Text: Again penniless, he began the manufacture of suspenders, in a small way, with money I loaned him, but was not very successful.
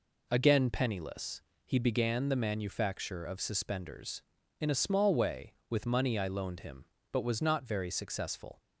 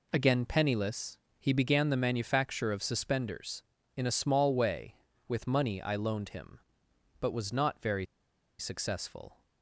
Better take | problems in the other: first | pauses between "very" and "successful"; noticeable; at 8.0 s; 0.54 s long

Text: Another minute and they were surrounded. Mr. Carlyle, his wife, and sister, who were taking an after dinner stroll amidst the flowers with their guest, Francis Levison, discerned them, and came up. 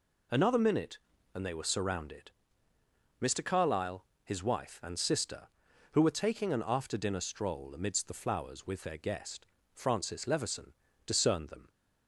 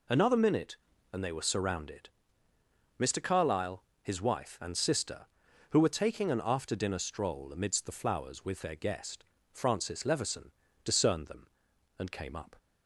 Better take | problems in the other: second | stops before "and came up"; at 11.6 s

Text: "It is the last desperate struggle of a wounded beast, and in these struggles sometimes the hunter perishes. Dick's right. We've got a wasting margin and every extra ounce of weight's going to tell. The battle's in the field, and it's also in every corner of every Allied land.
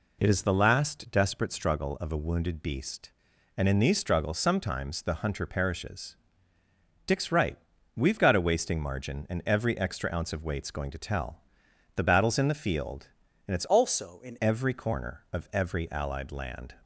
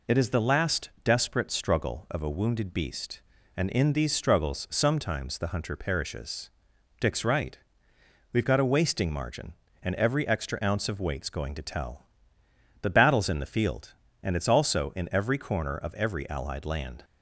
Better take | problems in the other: second | changes voice from "also" to "in"; from 13.6 to 14.3 s; 0.7 s long

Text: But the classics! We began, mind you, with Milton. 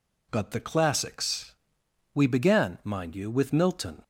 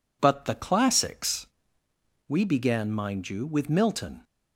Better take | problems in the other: neither | none

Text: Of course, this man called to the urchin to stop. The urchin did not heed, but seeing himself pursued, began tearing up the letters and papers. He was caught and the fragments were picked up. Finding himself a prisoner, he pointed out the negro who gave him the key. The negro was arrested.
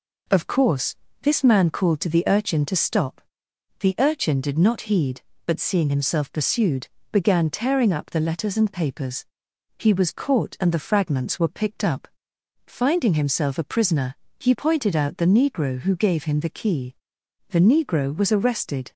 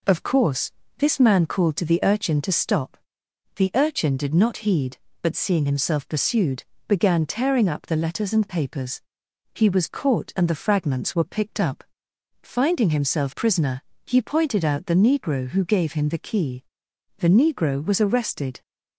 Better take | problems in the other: first | skips "a"; at 13.3 s

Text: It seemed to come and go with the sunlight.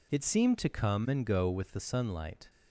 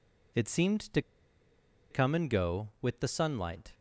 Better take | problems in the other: first | pauses between "to" and "come"; noticeable; at 1.0 s; 0.90 s long

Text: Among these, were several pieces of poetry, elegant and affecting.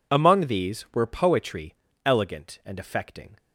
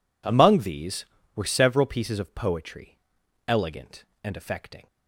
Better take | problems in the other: second | skips "several pieces of"; at 1.0 s

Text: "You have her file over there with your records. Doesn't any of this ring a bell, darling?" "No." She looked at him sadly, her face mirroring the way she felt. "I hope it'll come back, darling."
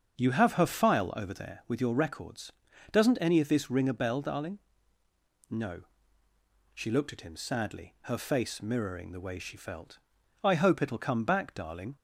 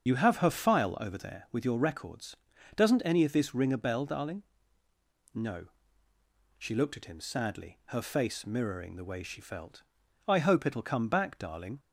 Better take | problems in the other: first | loses the start of "You"; at 0.0 s; 45 ms // starts louder than the rest; until 1.1 s; 7 dB; also in the first

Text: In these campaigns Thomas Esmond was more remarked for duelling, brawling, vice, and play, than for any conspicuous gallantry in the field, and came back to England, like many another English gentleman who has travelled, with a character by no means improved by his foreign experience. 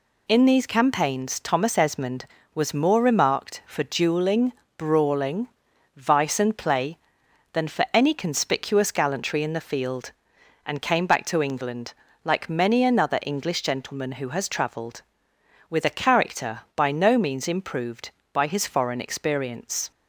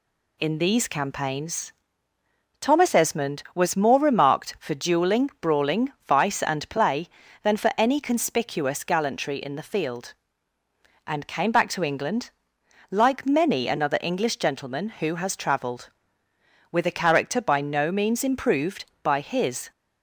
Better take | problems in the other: first | pauses between "campaigns" and "Thomas"; noticeable; at 1.7 s; 0.88 s long // stops before "foreign experience"; at 19.7 s

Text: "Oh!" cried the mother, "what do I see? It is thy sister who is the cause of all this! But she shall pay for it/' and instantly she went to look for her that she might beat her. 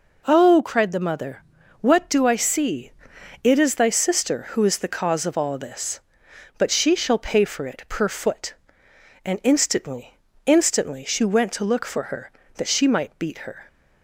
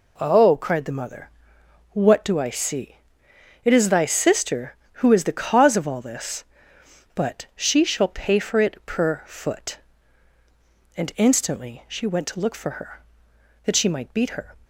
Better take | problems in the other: second | says "instantly" twice; at 10.4 s

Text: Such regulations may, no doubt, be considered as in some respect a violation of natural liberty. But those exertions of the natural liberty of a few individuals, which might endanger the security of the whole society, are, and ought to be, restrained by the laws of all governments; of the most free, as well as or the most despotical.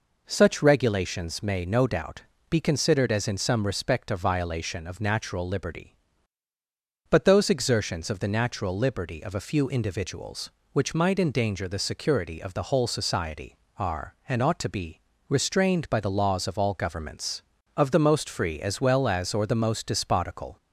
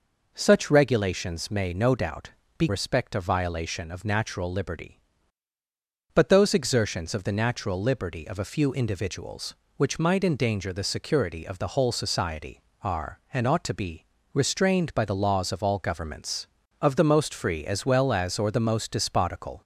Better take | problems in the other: first | skips "considered as in some"; at 2.6 s

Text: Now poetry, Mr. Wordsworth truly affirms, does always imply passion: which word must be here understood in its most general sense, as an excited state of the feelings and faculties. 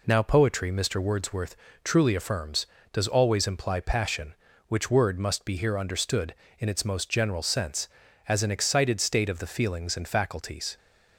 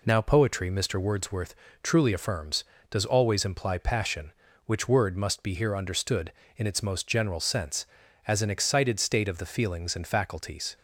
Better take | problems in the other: neither | pauses between "Wordsworth" and "truly"; slight; the same in both

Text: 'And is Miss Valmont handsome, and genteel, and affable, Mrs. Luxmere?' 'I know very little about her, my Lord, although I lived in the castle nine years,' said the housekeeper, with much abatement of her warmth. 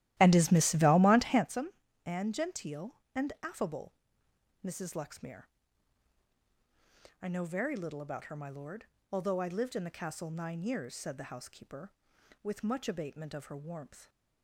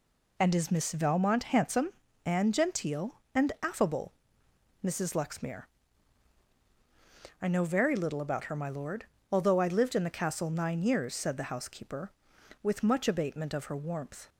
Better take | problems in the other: second | starts louder than the rest; strong; until 1.5 s; 14.5 dB

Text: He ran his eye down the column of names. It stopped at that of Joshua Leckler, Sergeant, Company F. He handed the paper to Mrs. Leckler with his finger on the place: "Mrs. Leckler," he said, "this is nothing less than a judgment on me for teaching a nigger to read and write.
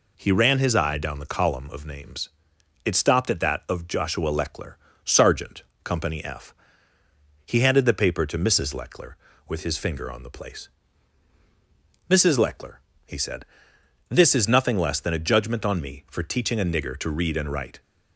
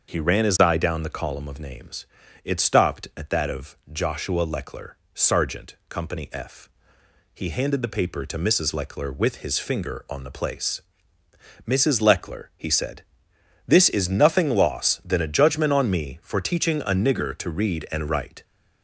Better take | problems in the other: first | starts louder than the rest; until 1.1 s; 6.5 dB // says "loss" for "less"; at 14.4 s

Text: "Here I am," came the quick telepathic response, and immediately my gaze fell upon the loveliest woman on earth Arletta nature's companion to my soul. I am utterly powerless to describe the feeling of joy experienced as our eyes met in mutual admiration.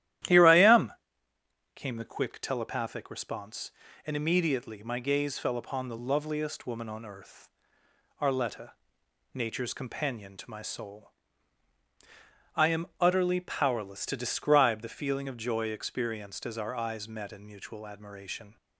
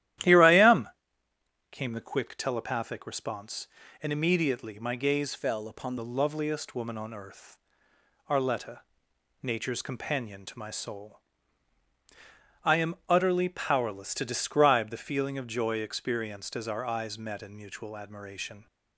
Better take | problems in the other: first | starts louder than the rest; strong; until 2.0 s; 13 dB; strong in the first // changes voice from "fell" to "upon"; from 5.3 to 5.9 s; 0.6 s long // pauses between "earth" and "Arletta"; noticeable; at 7.5 s; 0.70 s long; noticeable in the first // pauses between "Arletta" and "nature's"; noticeable; at 8.8 s; 0.60 s long; noticeable in the first

